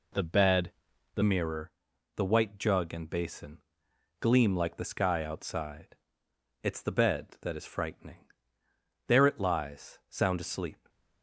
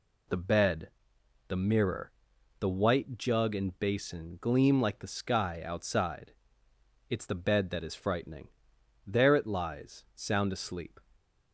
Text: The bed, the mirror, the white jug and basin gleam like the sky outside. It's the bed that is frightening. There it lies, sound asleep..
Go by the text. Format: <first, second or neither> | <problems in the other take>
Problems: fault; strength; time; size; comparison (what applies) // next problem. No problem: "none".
second | changes voice at "mirror"; from 1.2 s on; 9.6 s long // pauses between "basin" and "gleam"; noticeable; at 3.5 s; 0.60 s long